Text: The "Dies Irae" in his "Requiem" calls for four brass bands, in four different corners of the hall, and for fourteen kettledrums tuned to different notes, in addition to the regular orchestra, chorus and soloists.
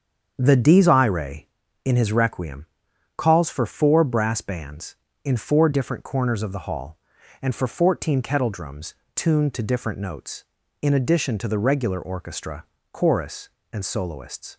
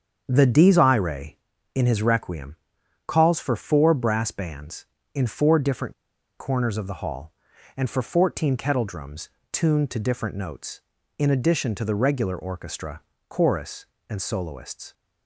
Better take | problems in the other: first | starts louder than the rest; strong; until 1.2 s; 7.5 dB; strong in the first // pauses between "Requiem" and "calls"; noticeable; at 2.5 s; 0.52 s long; noticeable in the first // pauses between "different" and "corners"; at 5.9 s; 0.45 s long // pauses between "kettledrums" and "tuned"; slight; at 9.2 s; 0.24 s long; slight in the first

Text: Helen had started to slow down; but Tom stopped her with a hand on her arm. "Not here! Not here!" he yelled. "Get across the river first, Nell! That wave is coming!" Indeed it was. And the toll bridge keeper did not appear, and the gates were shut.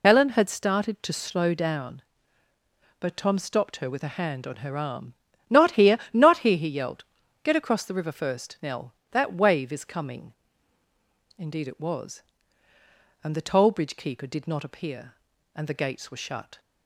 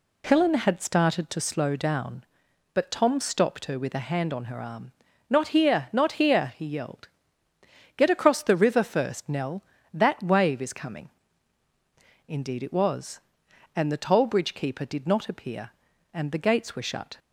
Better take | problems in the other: second | loses the start of "Helen"; at 0.0 s; 45 ms

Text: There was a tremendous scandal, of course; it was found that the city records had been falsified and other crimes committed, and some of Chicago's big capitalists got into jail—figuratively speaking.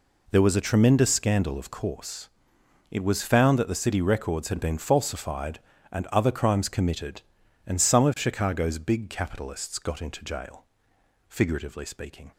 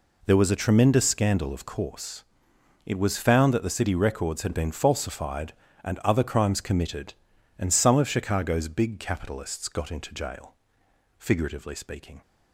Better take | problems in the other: neither | none

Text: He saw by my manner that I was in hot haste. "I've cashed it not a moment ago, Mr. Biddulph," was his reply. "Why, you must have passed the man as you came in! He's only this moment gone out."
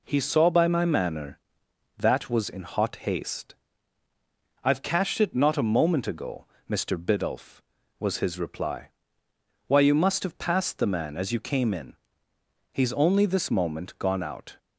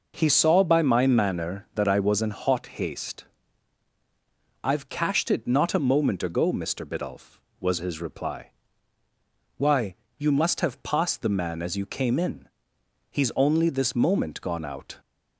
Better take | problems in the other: second | skips "I"; at 2.2 s

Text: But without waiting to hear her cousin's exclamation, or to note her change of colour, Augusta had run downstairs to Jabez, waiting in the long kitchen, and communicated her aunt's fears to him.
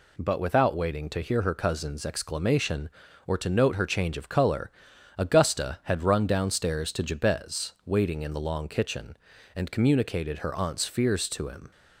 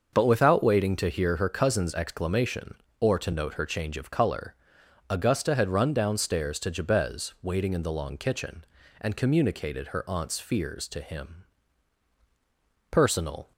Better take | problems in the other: first | starts louder than the rest; until 1.1 s; 6.5 dB // goes on to say "Personal"; from 12.9 s on; 0.60 s long

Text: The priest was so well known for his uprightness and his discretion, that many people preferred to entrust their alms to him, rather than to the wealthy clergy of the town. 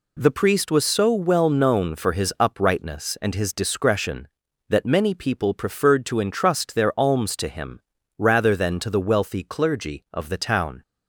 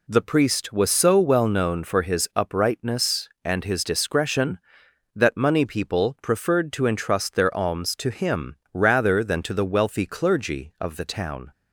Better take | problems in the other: first | says "money" for "many"; at 5.3 s

